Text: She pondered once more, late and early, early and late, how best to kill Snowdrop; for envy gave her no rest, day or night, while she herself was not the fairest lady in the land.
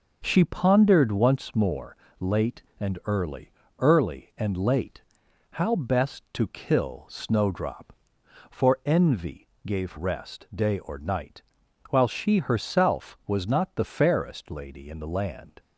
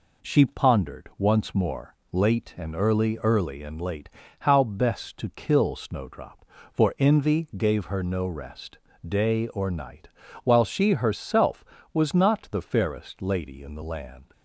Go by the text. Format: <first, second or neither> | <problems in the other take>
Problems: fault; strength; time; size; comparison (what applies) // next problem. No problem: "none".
second | pauses between "envy" and "gave"; slight; at 9.4 s; 0.18 s long // skips "her no"; at 9.9 s